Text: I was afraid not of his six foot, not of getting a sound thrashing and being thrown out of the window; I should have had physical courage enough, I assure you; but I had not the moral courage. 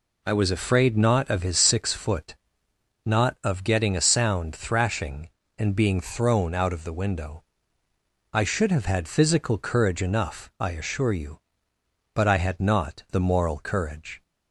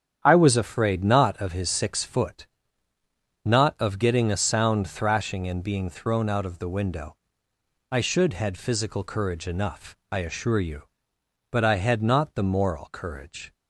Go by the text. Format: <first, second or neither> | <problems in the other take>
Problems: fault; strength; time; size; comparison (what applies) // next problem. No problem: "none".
first | starts louder than the rest; strong; until 1.2 s; 9 dB // skips "have"; at 8.3 s